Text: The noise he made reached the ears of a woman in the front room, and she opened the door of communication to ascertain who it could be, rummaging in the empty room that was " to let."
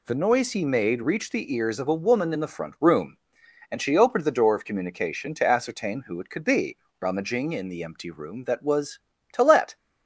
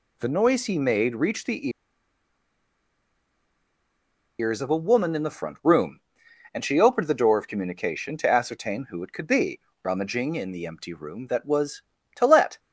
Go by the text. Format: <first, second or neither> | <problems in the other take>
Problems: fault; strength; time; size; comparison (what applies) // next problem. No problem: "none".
first | pauses between "the" and "ears"; strong; at 1.6 s; 2.7 s long